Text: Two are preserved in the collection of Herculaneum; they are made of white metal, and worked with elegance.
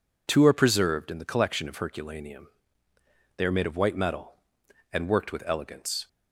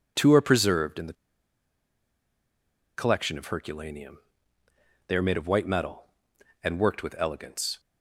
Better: first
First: none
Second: pauses between "the" and "collection"; strong; at 1.1 s; 1.8 s long

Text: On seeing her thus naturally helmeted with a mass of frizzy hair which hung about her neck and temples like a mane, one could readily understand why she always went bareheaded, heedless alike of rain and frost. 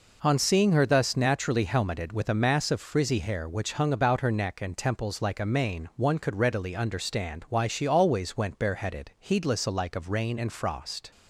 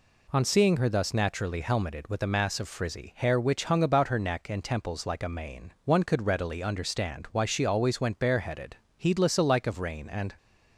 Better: first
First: none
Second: stops before "frost"; at 10.3 s

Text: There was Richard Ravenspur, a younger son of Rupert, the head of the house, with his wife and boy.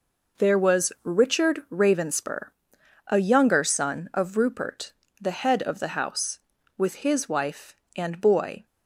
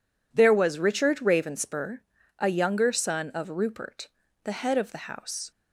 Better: first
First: none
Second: stops before "with his wife and boy"; at 5.5 s

